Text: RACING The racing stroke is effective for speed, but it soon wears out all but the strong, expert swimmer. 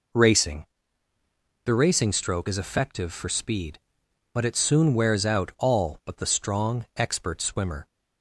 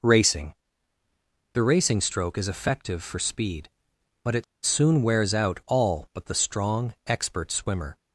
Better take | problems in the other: first | pauses between "RACING" and "The"; noticeable; at 0.5 s; 0.98 s long; noticeable in the first // pauses between "it" and "soon"; slight; at 4.4 s; 0.20 s long

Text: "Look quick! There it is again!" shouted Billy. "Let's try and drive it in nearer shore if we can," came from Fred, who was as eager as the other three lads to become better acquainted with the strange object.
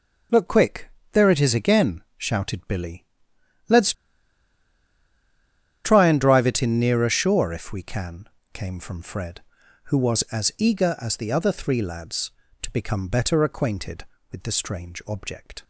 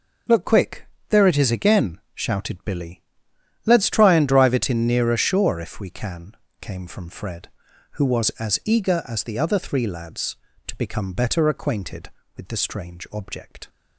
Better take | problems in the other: second | pauses between "Let's" and "try"; strong; at 3.9 s; 1.9 s long

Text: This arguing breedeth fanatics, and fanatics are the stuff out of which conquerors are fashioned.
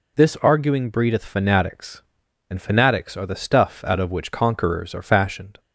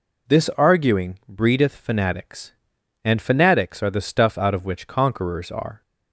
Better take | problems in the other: first | stops before "fashioned"; at 5.8 s

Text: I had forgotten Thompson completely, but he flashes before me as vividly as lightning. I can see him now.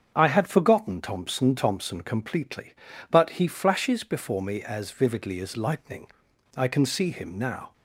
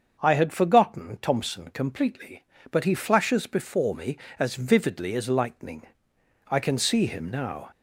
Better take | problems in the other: second | starts louder than the rest; strong; until 1.1 s; 7.5 dB; also in the second // says "Thompson" twice; at 1.5 s

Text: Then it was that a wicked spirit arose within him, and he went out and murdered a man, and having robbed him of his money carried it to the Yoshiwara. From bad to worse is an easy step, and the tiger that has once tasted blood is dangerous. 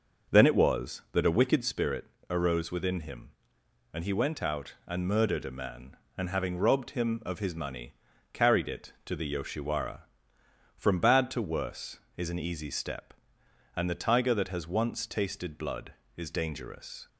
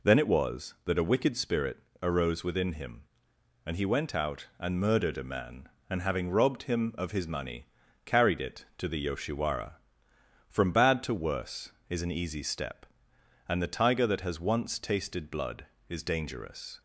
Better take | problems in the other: second | starts louder than the rest; noticeable; until 1.7 s; 6 dB // pauses between "spirit" and "arose"; slight; at 2.0 s; 0.24 s long; slight in the second // pauses between "money" and "carried"; at 7.9 s; 0.40 s long; also in the second

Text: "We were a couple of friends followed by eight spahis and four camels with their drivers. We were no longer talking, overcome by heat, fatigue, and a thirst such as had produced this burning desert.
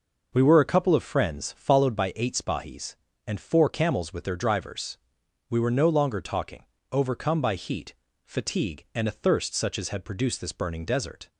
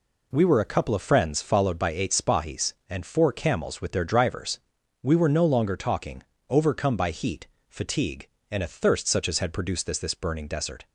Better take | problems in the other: first | says "this" twice; at 9.9 s

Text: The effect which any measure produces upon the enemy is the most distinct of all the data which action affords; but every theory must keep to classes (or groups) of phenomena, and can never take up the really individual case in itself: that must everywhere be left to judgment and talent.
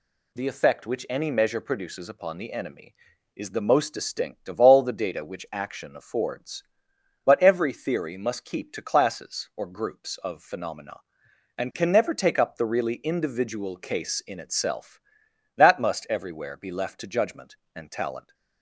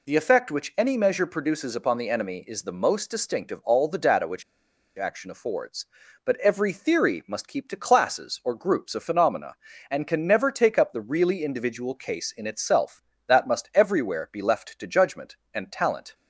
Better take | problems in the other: first | pauses between "which" and "action"; noticeable; at 4.4 s; 0.55 s long

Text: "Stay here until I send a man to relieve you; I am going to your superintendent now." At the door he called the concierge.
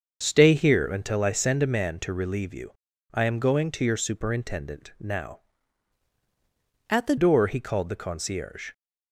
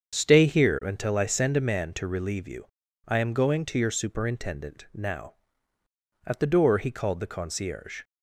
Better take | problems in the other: second | starts louder than the rest; until 1.2 s; 6.5 dB; strong in the second // changes voice from "At" to "the"; from 6.8 to 7.1 s; 0.3 s long

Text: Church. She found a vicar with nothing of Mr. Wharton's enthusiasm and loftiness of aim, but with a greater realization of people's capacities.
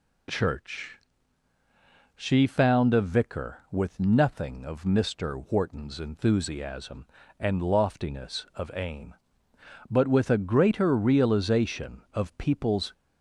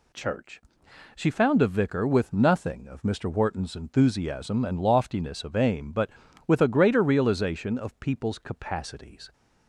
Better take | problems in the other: second | stops before "capacities"; at 12.9 s

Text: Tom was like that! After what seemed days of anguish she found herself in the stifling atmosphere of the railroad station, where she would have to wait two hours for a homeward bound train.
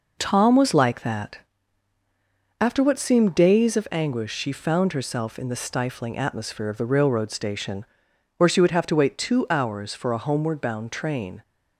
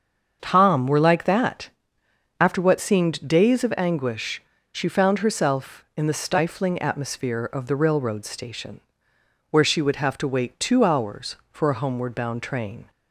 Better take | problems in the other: first | starts louder than the rest; until 1.4 s; 7 dB // says "were" for "was"; at 0.8 s // pauses between "anguish" and "she"; slight; at 4.4 s; 0.31 s long

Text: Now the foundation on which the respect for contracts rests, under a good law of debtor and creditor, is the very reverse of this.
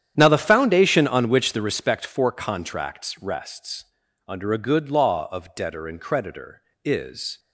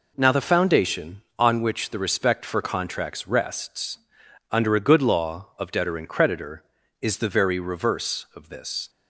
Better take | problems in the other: second | starts louder than the rest; strong; until 1.1 s; 9.5 dB // stops before "the very reverse of this"; at 7.3 s

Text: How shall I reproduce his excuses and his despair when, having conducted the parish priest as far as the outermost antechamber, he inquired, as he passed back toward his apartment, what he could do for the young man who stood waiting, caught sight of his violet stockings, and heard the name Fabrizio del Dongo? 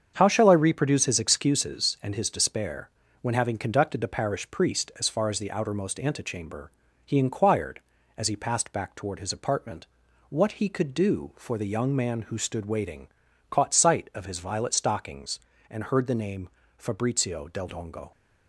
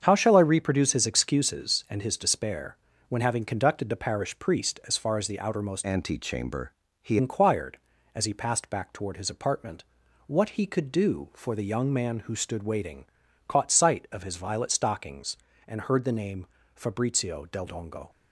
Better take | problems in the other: first | starts louder than the rest; strong; until 1.0 s; 7.5 dB; strong in the first // pauses between "despair" and "when"; slight; at 2.7 s; 0.32 s long; slight in the first // changes voice from "antechamber" to "he"; from 5.8 to 7.1 s; 1.3 s long // pauses between "name" and "Fabrizio"; slight; at 16.4 s; 0.26 s long; slight in the first

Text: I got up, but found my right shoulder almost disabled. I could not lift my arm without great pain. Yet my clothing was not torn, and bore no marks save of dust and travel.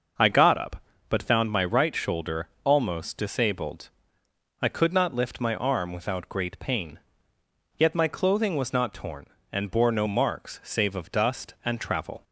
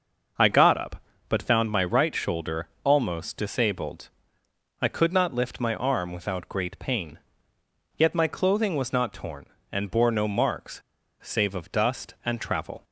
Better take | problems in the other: first | starts louder than the rest; noticeable; until 1.6 s; 6 dB; noticeable in the first // pauses between "shoulder" and "almost"; slight; at 2.6 s; 0.16 s long; slight in the first // pauses between "marks" and "save"; at 10.8 s; 0.40 s long

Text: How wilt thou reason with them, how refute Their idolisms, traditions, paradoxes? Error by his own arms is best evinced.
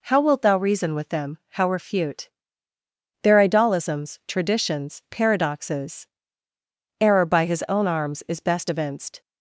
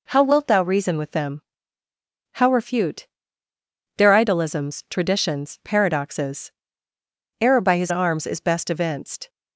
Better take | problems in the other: first | pauses between "refute" and "Their"; noticeable; at 3.0 s; 0.90 s long; noticeable in the first // skips "own"; at 7.9 s

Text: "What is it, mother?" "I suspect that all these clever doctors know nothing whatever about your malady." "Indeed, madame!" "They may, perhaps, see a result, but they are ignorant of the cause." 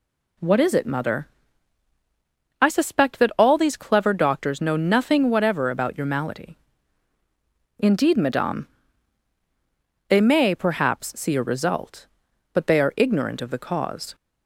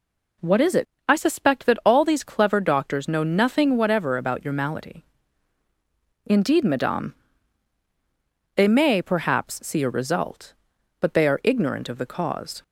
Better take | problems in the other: first | skips "mother"; at 0.9 s

